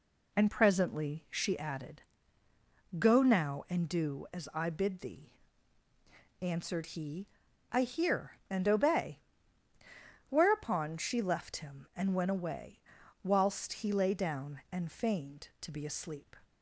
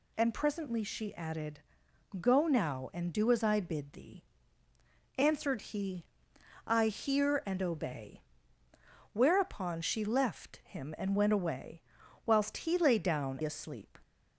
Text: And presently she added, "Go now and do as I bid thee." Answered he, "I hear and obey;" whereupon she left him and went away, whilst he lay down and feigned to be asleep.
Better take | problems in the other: first | skips "and feigned to be"; at 13.4 s

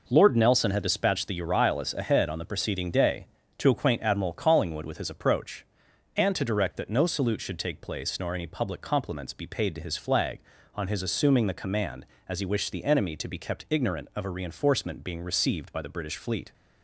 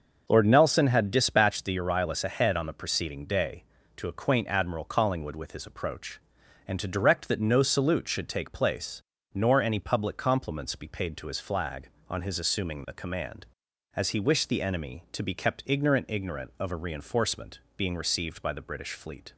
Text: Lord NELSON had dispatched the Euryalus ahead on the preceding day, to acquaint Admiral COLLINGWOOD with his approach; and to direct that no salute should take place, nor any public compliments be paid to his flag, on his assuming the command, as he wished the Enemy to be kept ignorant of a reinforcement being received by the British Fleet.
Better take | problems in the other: first | starts louder than the rest; until 1.2 s; 6.5 dB // says "ignorant" twice; at 16.0 s // pauses between "reinforcement" and "being"; slight; at 17.5 s; 0.18 s long

